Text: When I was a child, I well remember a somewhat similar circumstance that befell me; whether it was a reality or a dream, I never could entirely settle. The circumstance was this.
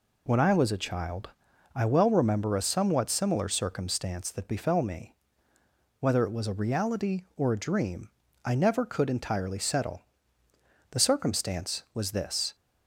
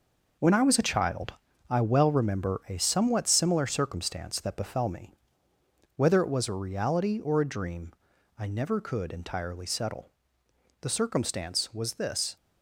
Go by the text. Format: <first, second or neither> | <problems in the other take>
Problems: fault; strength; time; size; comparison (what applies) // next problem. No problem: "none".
first | gets quieter; strong; throughout; 8.5 dB